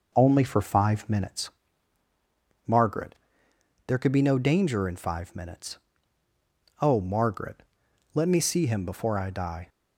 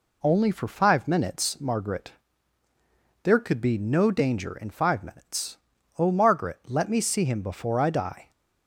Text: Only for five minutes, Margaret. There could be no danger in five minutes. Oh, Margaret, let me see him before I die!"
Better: second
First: starts louder than the rest; noticeable; until 1.5 s; 5 dB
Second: none

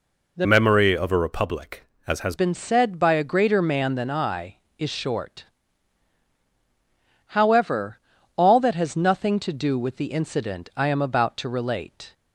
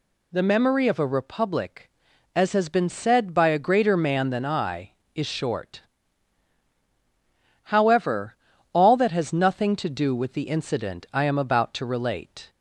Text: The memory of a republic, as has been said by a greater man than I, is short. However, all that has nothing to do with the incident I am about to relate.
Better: second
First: changes voice from "memory" to "has"; from 0.4 to 2.3 s; 1.9 s long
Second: none

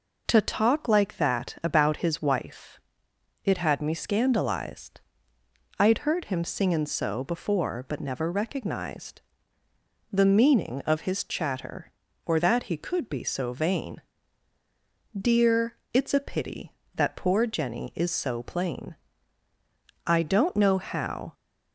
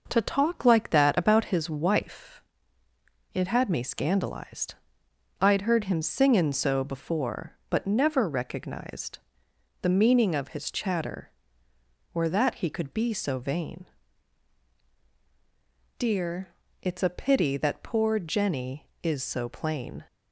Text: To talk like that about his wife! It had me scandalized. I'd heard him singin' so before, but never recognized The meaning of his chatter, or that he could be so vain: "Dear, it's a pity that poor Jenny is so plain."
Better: second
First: pauses between "recognized" and "The"; noticeable; at 9.2 s; 0.90 s long // goes on to say "I don't know how"; noticeable; from 20.0 s on; 1.2 s long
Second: pauses between "recognized" and "The"; noticeable; at 9.1 s; 0.64 s long

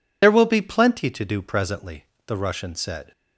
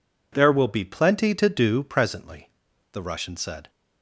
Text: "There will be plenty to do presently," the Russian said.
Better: second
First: loses the start of "There"; at 0.2 s; 50 ms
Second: none

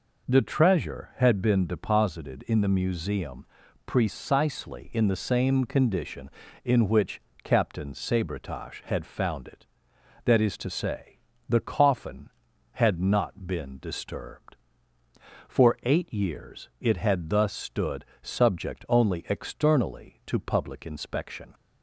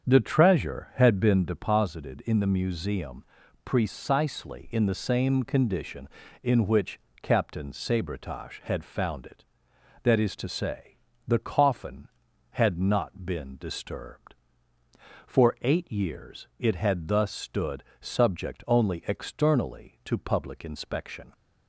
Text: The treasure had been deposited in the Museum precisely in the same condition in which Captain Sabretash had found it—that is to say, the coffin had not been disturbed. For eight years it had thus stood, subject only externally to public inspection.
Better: first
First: pauses between "Museum" and "precisely"; at 3.4 s; 0.40 s long // pauses between "which" and "Captain"; slight; at 7.1 s; 0.24 s long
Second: starts louder than the rest; strong; until 1.6 s; 7.5 dB // pauses between "Museum" and "precisely"; at 3.2 s; 0.40 s long // pauses between "which" and "Captain"; slight; at 6.9 s; 0.24 s long

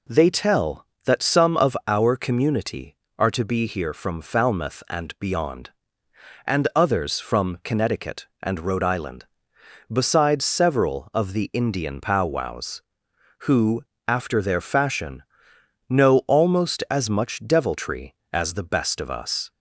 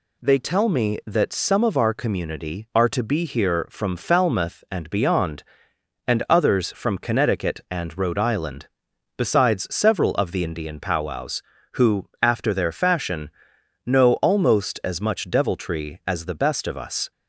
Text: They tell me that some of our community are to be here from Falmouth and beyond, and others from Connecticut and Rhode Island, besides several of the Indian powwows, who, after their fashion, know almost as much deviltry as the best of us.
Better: second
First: skips "me"; at 0.9 s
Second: none

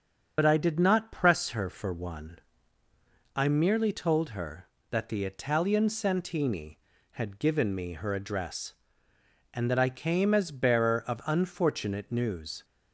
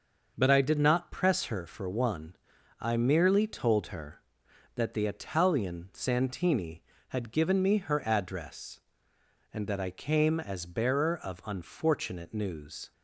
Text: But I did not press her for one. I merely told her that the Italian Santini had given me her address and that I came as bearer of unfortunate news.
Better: second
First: loses the start of "But"; at 0.3 s; 60 ms // starts louder than the rest; until 1.3 s; 6.5 dB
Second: starts louder than the rest; noticeable; until 1.3 s; 6 dB

